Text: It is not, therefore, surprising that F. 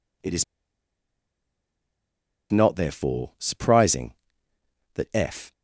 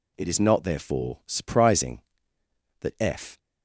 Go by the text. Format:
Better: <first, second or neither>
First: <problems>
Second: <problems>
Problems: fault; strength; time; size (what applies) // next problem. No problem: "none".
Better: second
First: pauses between "is" and "not"; strong; at 0.4 s; 2.0 s long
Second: none